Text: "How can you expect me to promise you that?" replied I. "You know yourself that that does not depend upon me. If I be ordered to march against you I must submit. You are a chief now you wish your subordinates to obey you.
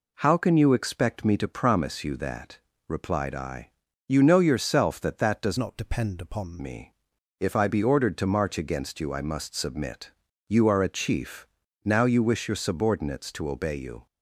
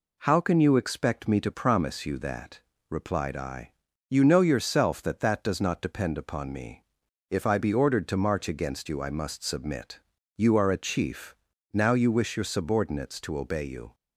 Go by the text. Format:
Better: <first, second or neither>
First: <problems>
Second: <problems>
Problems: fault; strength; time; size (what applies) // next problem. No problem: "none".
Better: second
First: changes voice from "not" to "upon"; from 5.5 to 6.6 s; 1.1 s long // pauses between "chief" and "now"; at 11.4 s; 0.40 s long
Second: pauses between "chief" and "now"; at 11.3 s; 0.40 s long